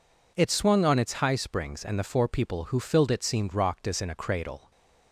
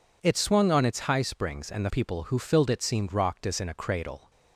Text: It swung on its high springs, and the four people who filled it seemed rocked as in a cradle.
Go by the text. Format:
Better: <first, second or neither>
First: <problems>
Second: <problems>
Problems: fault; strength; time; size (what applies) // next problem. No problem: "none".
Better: first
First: none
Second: skips "four"; at 1.8 s